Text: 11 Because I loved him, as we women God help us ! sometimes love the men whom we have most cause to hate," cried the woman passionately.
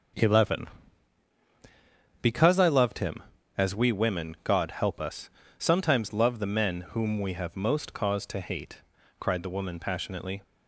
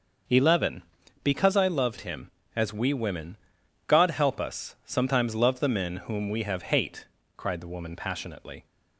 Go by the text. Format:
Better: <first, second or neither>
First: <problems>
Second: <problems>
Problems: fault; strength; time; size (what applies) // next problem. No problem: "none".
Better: first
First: starts louder than the rest; until 2.7 s; 6.5 dB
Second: starts louder than the rest; until 1.6 s; 6 dB // pauses between "women" and "God"; noticeable; at 3.3 s; 0.48 s long // skips "most cause to"; at 6.7 s